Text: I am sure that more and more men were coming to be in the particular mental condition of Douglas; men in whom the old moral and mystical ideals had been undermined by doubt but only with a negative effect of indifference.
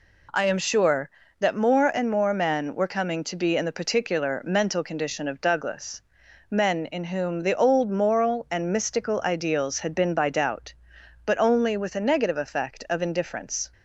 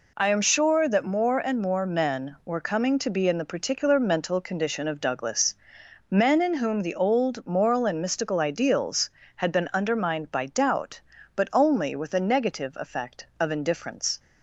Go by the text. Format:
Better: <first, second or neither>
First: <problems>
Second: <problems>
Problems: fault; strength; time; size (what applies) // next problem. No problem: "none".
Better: second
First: skips "undermined"; at 10.1 s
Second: none